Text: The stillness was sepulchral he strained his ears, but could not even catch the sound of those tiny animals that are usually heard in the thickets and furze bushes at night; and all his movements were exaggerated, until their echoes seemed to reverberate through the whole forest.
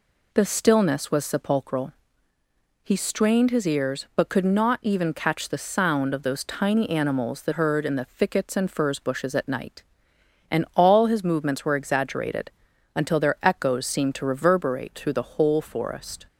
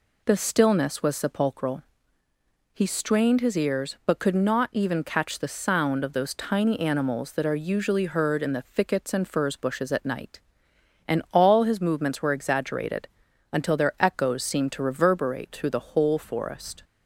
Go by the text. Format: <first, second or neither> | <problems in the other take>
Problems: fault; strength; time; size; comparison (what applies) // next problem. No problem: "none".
second | pauses between "sepulchral" and "he"; noticeable; at 1.9 s; 0.92 s long; noticeable in the second // skips "are usually"; at 7.5 s